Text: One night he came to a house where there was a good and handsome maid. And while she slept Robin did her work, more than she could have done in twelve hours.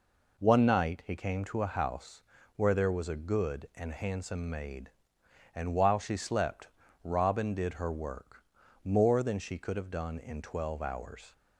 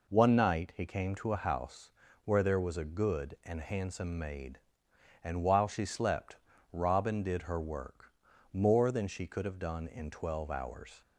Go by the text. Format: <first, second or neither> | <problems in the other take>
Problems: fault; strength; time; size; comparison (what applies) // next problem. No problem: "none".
neither | pauses between "house" and "where"; slight; the same in both // pauses between "slept" and "Robin"; slight; the same in both